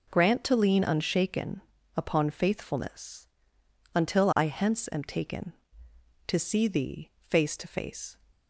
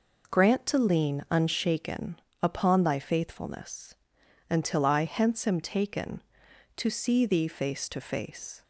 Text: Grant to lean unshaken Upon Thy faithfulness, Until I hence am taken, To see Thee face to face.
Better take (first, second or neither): second